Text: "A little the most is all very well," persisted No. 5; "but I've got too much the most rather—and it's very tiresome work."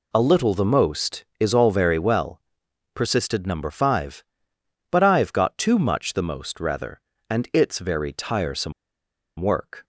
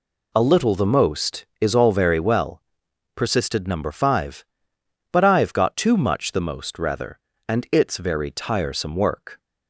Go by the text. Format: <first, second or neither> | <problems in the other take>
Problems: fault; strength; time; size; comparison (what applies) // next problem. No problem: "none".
second | pauses between "tiresome" and "work"; noticeable; at 8.7 s; 0.67 s long